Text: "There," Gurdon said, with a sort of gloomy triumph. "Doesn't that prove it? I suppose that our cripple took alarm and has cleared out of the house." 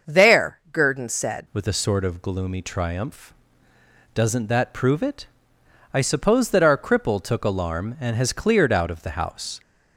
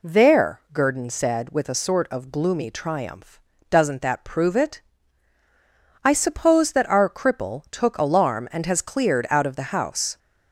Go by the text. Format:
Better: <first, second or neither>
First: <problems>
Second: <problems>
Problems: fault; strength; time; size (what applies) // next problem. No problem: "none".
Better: second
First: starts louder than the rest; until 1.1 s; 6.5 dB // changes voice at "with"; from 1.5 s on; 8.0 s long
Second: none